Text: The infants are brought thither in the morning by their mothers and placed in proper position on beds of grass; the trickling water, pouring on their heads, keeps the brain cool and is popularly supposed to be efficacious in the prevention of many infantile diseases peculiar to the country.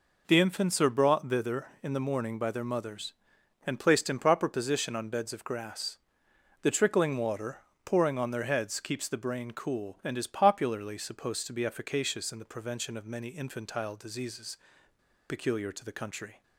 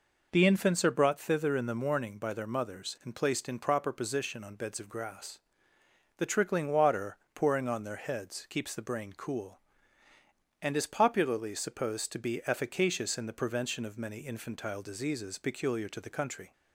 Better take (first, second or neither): second